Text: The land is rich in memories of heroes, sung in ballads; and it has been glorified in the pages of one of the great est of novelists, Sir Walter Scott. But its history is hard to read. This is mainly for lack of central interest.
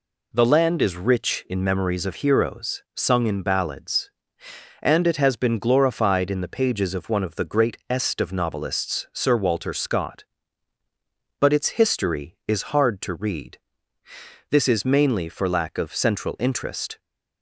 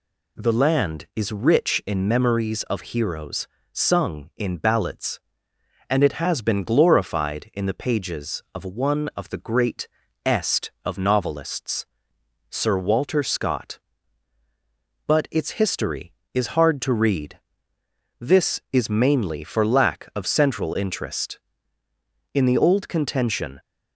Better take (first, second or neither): first